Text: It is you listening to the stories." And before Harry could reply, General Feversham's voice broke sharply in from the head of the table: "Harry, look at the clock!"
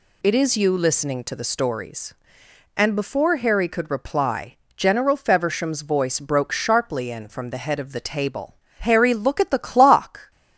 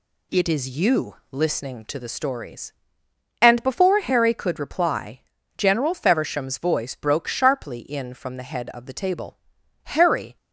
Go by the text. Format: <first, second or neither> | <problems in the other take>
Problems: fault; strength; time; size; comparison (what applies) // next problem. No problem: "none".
first | pauses between "you" and "listening"; slight; at 1.1 s; 0.16 s long // stops before "look at the clock"; at 10.3 s